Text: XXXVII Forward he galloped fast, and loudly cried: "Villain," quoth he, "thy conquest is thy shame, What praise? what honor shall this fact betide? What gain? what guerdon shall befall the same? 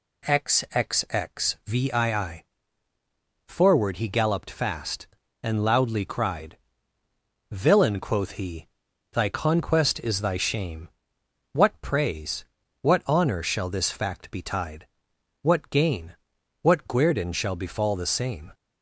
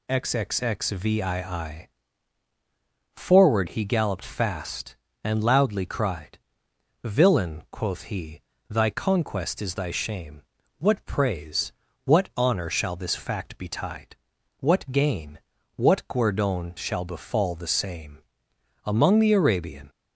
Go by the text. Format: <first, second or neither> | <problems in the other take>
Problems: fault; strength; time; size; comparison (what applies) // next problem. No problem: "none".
first | pauses between "XXXVII" and "Forward"; strong; at 1.8 s; 1.2 s long; also in the first // goes on to say "Among the Arabian"; noticeable; from 18.8 s on; 1.0 s long